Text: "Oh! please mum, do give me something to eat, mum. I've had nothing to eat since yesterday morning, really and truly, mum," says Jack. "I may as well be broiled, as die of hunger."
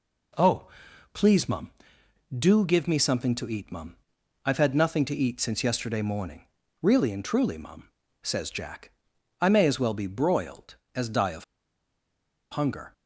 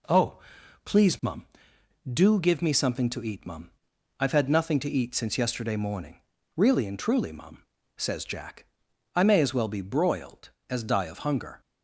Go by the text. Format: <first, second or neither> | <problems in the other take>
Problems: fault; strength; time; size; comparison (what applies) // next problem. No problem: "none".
second | pauses between "of" and "hunger"; at 11.4 s; 1.0 s long